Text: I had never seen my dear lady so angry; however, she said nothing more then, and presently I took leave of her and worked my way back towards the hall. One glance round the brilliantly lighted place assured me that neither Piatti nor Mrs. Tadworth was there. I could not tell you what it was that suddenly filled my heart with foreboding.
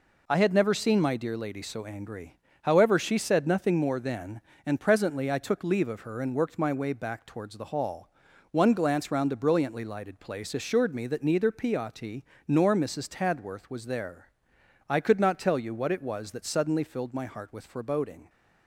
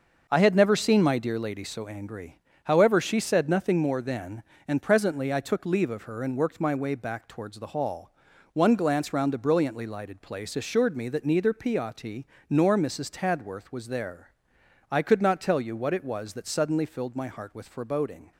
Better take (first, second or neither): first